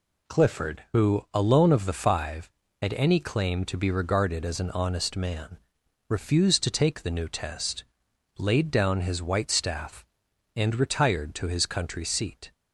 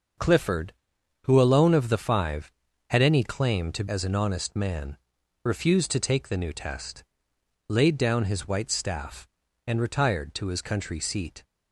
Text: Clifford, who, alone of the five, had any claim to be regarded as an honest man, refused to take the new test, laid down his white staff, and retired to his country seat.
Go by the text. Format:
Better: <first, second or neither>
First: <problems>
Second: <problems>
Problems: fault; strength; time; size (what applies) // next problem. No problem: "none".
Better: first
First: none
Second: starts louder than the rest; until 1.6 s; 6.5 dB // skips "be regarded"; at 3.8 s